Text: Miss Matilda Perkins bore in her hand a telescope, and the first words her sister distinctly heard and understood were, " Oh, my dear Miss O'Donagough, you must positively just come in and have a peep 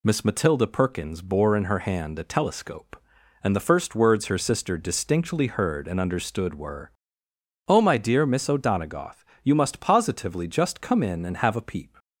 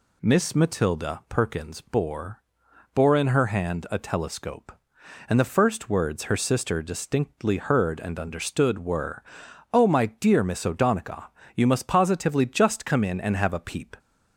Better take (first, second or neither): first